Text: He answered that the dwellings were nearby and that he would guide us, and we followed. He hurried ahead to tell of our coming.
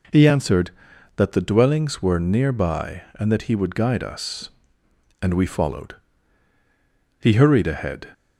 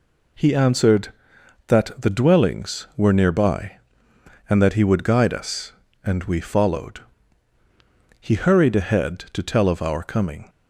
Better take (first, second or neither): second